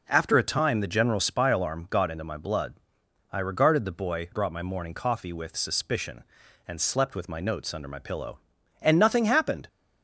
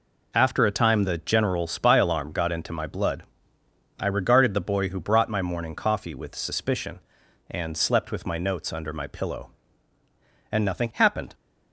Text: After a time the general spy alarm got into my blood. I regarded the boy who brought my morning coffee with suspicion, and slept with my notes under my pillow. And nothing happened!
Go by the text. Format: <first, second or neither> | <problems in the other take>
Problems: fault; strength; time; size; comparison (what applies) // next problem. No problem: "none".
second | skips "who"; at 4.3 s